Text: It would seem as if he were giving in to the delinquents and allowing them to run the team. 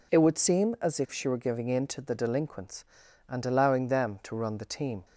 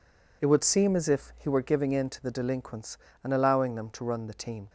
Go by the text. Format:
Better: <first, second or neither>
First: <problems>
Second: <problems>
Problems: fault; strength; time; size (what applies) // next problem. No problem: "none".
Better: second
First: says "she" for "he"; at 1.1 s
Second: none